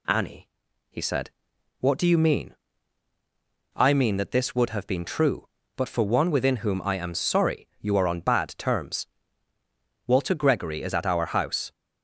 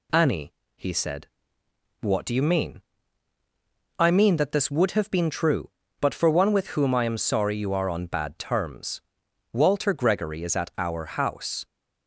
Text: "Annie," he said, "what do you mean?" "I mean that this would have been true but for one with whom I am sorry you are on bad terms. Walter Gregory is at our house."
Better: second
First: says "within" for "with"; at 6.2 s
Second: none

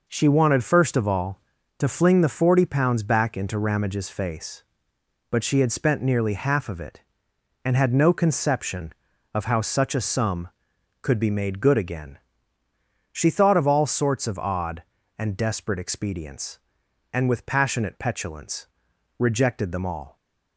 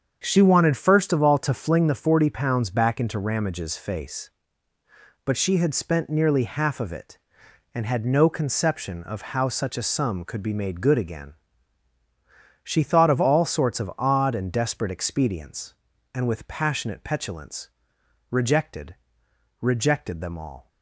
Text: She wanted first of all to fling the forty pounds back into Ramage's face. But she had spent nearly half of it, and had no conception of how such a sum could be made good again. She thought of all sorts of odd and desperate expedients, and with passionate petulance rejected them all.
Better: first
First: pauses between "petulance" and "rejected"; noticeable; at 18.6 s; 0.52 s long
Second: starts louder than the rest; strong; until 1.2 s; 7.5 dB // pauses between "petulance" and "rejected"; noticeable; at 17.7 s; 0.60 s long // says "rejected" twice; at 19.6 s

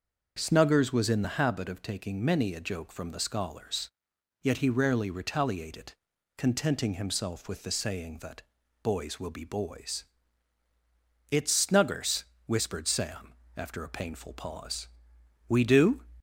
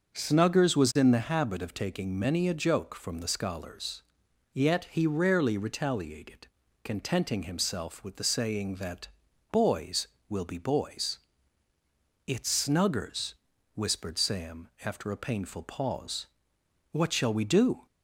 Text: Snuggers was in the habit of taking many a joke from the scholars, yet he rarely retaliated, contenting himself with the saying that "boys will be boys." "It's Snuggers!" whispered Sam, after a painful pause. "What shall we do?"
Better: second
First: starts louder than the rest; until 1.3 s; 6 dB // pauses between "that" and "boys"; at 8.4 s; 0.40 s long // skips "What shall"; at 15.1 s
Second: starts louder than the rest; until 1.1 s; 6.5 dB // pauses between "that" and "boys"; at 9.0 s; 0.44 s long

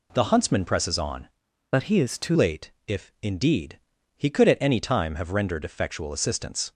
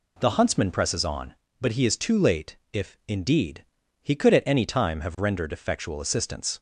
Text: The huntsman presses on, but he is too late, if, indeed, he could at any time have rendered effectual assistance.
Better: second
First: changes voice from "but" to "too"; from 1.7 to 2.3 s; 0.6 s long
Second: none

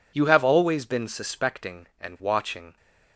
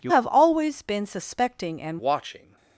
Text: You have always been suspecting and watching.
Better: first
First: none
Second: changes voice from "have" to "and"; from 0.0 to 1.9 s; 1.9 s long

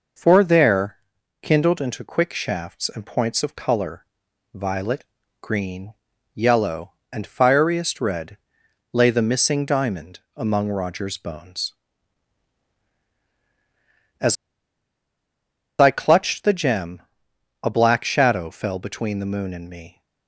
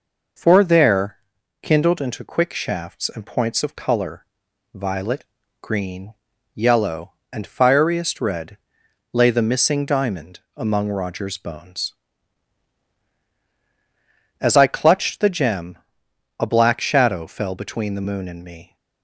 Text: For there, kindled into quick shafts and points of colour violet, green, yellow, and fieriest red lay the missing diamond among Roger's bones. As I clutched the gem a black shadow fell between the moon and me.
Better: second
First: pauses between "colour" and "violet"; at 4.0 s; 0.44 s long // pauses between "red" and "lay"; noticeable; at 8.3 s; 0.54 s long // pauses between "As" and "I"; strong; at 14.3 s; 1.4 s long // pauses between "gem" and "a"; noticeable; at 16.9 s; 0.62 s long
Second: pauses between "colour" and "violet"; at 4.2 s; 0.44 s long // pauses between "red" and "lay"; noticeable; at 8.5 s; 0.54 s long // pauses between "gem" and "a"; noticeable; at 15.7 s; 0.62 s long

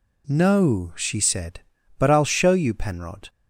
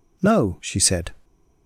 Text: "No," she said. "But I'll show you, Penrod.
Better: first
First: none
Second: stops before "But I'll show you Penrod"; at 1.2 s

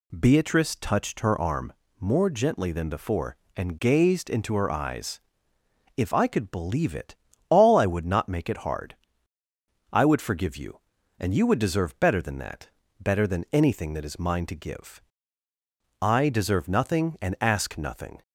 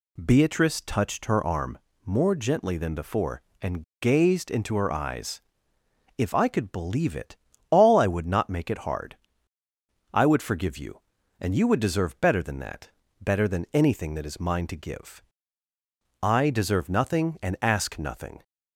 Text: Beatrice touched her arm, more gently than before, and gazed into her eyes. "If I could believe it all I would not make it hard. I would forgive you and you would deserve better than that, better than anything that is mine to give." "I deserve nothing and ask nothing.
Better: first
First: pauses between "it" and "all"; slight; at 7.1 s; 0.34 s long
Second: pauses between "and" and "gazed"; slight; at 3.8 s; 0.20 s long // pauses between "it" and "all"; slight; at 7.3 s; 0.34 s long

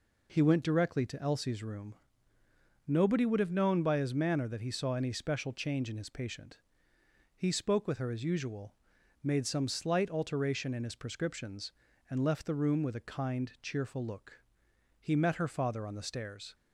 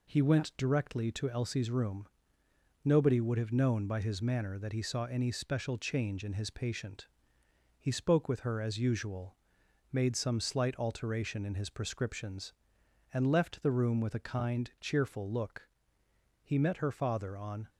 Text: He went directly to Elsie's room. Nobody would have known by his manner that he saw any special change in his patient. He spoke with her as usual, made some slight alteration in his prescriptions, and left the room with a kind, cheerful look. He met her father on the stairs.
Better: first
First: none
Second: stops before "the stairs"; at 17.6 s

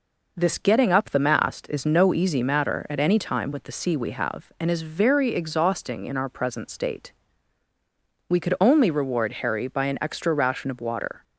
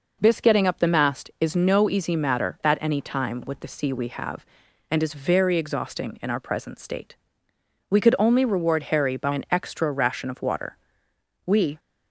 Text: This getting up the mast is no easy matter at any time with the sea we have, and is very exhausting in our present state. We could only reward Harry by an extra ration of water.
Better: first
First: none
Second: goes on to say "We"; slight; from 11.4 s on; 0.34 s long

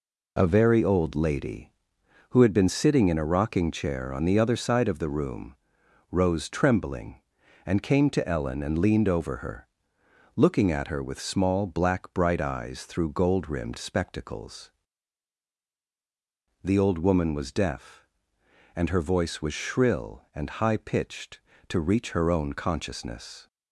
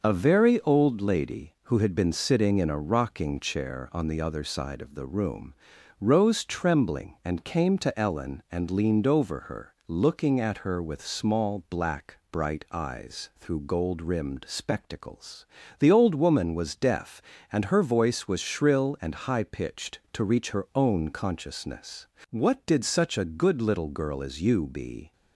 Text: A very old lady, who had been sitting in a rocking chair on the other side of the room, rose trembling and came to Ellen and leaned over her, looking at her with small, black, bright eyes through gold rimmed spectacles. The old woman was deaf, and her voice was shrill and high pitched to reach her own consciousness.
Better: first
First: none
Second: starts louder than the rest; until 1.0 s; 6 dB // goes on to say "What did such a good little girl as you be"; strong; from 22.2 s on; 2.8 s long

